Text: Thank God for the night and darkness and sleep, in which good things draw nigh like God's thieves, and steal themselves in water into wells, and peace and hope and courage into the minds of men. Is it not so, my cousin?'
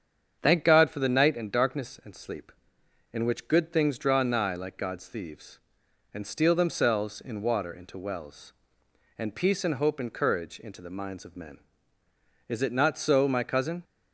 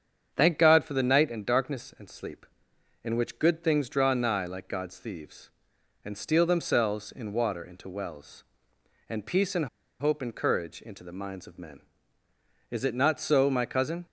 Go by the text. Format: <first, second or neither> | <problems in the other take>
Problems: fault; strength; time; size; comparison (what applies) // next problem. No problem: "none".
first | starts louder than the rest; strong; until 1.3 s; 7.5 dB; strong in the first // pauses between "and" and "hope"; slight; at 9.6 s; 0.33 s long